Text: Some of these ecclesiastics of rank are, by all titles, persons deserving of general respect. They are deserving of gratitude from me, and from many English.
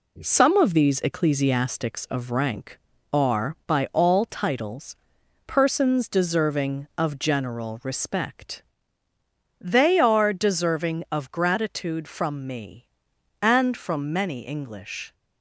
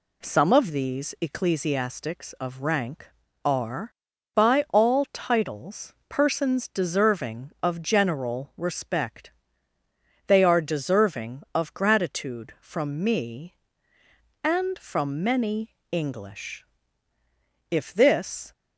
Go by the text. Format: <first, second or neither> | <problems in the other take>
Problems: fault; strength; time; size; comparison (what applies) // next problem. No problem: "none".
first | pauses between "many" and "English"; slight; at 15.7 s; 0.18 s long // goes on to say "If this"; noticeable; from 17.6 s on; 0.82 s long